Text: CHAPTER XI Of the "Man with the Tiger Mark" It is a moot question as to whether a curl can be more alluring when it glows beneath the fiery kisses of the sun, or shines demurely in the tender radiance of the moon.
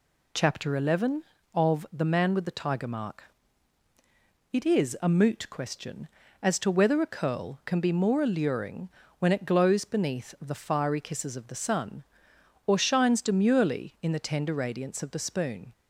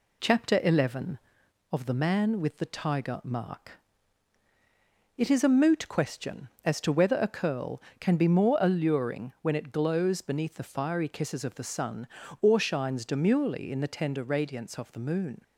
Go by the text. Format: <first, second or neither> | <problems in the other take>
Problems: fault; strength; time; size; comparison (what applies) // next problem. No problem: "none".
second | pauses between "Mark" and "It"; strong; at 3.2 s; 1.3 s long; strong in the second // pauses between "alluring" and "when"; slight; at 8.8 s; 0.30 s long // says "spoon" for "moon"; at 15.1 s